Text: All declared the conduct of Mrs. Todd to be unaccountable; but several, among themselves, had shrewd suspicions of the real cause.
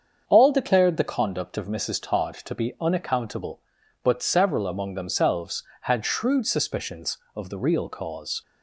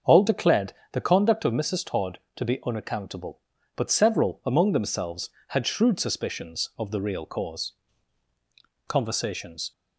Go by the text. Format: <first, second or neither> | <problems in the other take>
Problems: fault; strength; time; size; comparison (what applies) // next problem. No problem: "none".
first | starts louder than the rest; until 1.2 s; 6.5 dB; also in the first // pauses between "declared" and "the"; slight; at 0.7 s; 0.22 s long // goes on to say "Conversations"; noticeable; from 8.8 s on; 0.84 s long